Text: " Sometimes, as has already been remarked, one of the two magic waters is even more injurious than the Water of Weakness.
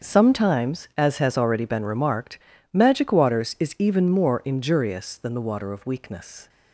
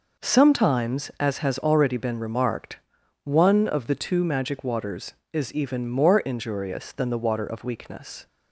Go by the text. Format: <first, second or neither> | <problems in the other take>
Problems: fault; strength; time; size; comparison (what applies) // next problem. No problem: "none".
second | starts louder than the rest; until 1.1 s; 6.5 dB // skips "one of the two"; at 2.5 s